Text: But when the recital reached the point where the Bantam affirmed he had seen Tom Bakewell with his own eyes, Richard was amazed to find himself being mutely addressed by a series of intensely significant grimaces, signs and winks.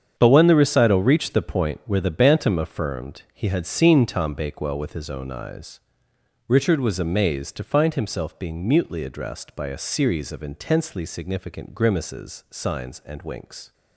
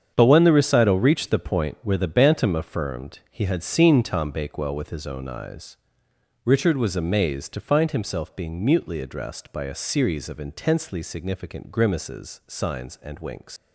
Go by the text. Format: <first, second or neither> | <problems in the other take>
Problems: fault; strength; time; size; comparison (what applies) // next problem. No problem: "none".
first | starts louder than the rest; strong; until 1.1 s; 8 dB; strong in the first // leaves "winks" unfinished; at 13.5 s; 135 ms